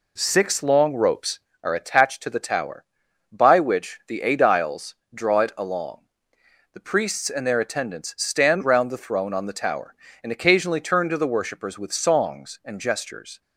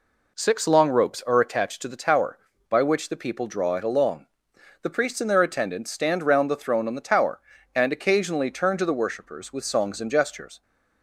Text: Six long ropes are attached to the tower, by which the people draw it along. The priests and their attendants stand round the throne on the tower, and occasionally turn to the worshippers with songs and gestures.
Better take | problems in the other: second | says "aediles" for "people"; at 4.2 s

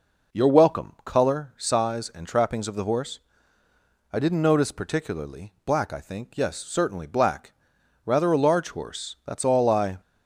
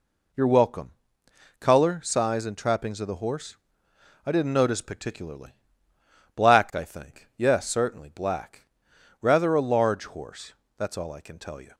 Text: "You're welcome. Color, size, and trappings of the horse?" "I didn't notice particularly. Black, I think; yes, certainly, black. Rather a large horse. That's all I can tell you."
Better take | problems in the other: second | stops before "can tell you"; at 10.0 s

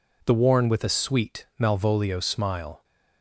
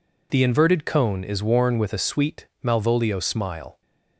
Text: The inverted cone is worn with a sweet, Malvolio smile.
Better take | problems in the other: second | skips "inverted cone is"; at 0.3 s

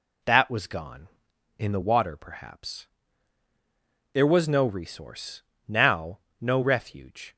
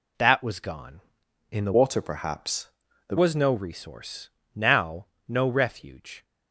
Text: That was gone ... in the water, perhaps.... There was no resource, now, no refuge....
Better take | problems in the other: first | changes voice from "water" to "There"; from 1.7 to 3.1 s; 1.4 s long

